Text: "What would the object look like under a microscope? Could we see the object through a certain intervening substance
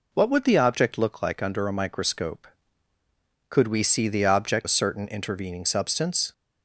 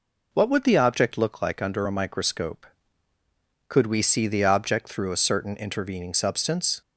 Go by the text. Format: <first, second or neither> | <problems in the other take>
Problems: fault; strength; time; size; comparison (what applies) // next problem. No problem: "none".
second | skips "through"; at 4.6 s